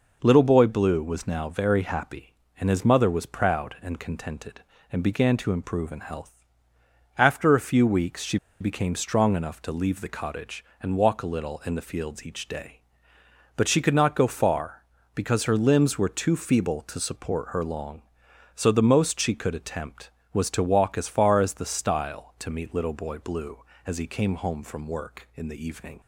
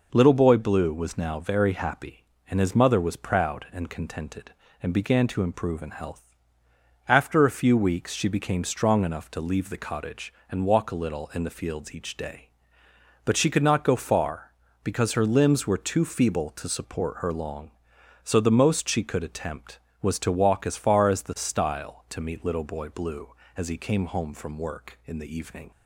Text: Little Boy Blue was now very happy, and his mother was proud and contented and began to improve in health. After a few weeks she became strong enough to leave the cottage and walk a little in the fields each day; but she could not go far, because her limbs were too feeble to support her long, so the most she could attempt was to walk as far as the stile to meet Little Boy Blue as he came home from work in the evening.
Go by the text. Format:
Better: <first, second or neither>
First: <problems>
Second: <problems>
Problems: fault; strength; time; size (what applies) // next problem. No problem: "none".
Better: second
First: pauses between "she" and "became"; slight; at 8.3 s; 0.23 s long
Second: none